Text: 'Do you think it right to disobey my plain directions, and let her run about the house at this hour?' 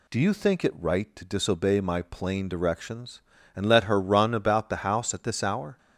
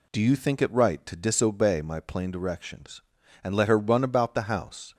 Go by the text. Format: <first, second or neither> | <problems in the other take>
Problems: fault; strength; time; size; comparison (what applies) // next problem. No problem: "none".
first | stops before "at this hour"; at 4.9 s